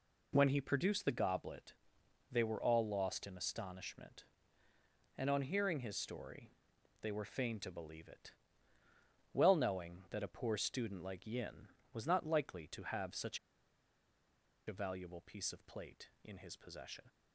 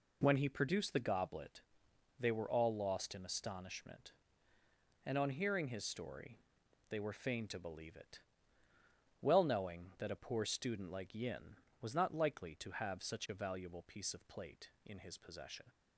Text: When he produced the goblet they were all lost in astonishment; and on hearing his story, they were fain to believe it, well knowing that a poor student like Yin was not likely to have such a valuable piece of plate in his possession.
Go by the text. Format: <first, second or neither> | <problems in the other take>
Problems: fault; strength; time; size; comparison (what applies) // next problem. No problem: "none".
second | pauses between "goblet" and "they"; noticeable; at 1.7 s; 0.54 s long; noticeable in the second // pauses between "such" and "a"; strong; at 13.3 s; 1.2 s long